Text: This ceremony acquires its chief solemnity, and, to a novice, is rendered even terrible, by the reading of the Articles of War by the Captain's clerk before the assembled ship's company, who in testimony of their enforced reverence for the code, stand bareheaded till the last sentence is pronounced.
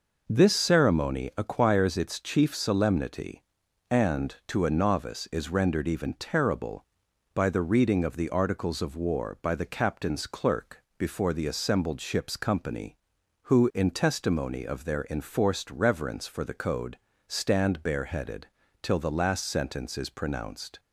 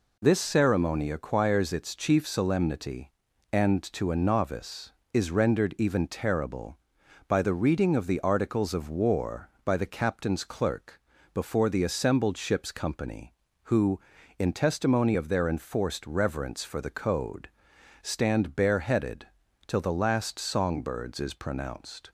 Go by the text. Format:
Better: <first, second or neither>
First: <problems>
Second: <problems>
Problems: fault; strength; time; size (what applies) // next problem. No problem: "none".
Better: first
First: pauses between "clerk" and "before"; slight; at 10.8 s; 0.16 s long // pauses between "bareheaded" and "till"; at 18.4 s; 0.38 s long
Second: pauses between "clerk" and "before"; slight; at 10.9 s; 0.36 s long // pauses between "bareheaded" and "till"; at 19.2 s; 0.40 s long // says "songbirds" for "sentence"; at 20.3 s